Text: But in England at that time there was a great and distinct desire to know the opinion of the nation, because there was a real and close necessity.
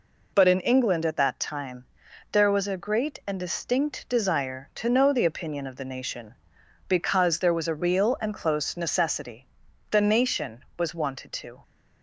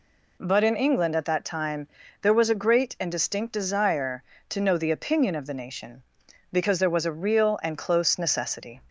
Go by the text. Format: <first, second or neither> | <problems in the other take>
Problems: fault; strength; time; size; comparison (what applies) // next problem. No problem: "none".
second | pauses between "time" and "there"; noticeable; at 1.8 s; 0.48 s long; slight in the second // goes on to say "The nation was wanted to"; strong; from 9.9 s on; 1.7 s long